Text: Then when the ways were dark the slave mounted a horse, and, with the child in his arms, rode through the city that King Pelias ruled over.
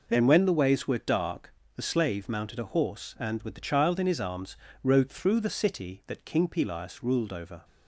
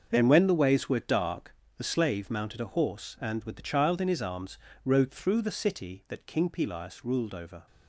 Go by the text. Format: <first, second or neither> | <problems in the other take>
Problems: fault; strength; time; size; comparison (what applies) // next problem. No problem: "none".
first | gets quieter; strong; throughout; 11 dB // pauses between "dark" and "the"; slight; at 1.5 s; 0.22 s long; slight in the first